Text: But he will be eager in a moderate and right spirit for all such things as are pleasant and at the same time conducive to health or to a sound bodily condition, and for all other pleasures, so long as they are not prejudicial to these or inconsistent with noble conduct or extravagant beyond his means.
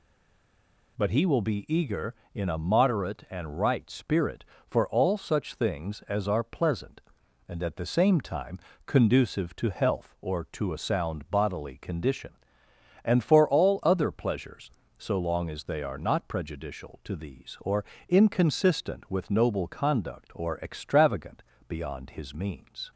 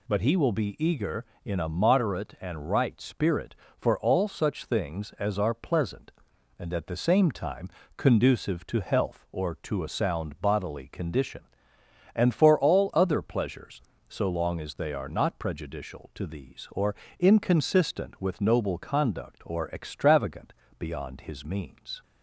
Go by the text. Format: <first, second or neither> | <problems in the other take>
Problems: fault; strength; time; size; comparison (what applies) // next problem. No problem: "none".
second | stays silent before the first word; slight; until 0.9 s; 0.9 s long // pauses between "time" and "conducive"; slight; at 8.5 s; 0.26 s long; slight in the second // pauses between "or" and "inconsistent"; slight; at 17.8 s; 0.26 s long; slight in the second // pauses between "extravagant" and "beyond"; slight; at 21.4 s; 0.24 s long; slight in the second